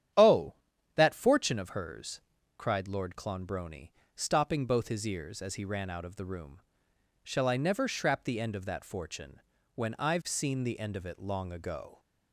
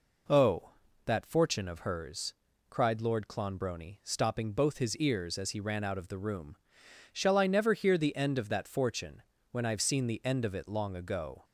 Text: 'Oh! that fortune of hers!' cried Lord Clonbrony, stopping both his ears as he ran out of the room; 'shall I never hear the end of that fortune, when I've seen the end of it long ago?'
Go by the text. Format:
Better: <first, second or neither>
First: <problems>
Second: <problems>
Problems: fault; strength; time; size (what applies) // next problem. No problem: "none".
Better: second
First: starts louder than the rest; strong; until 1.5 s; 10 dB // says "shrap" for "hear"; at 7.8 s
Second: none